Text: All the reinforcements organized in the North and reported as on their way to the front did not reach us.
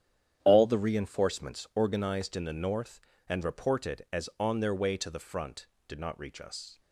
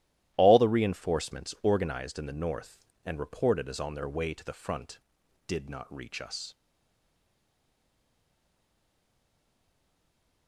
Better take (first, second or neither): first